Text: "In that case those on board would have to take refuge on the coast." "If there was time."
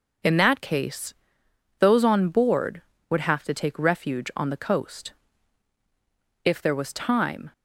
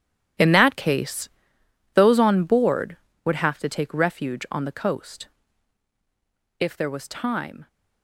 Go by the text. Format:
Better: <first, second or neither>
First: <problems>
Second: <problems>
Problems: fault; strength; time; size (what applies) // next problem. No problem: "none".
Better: first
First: pauses between "case" and "those"; noticeable; at 1.1 s; 0.64 s long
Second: gets quieter; strong; throughout; 13.5 dB // pauses between "case" and "those"; noticeable; at 1.2 s; 0.64 s long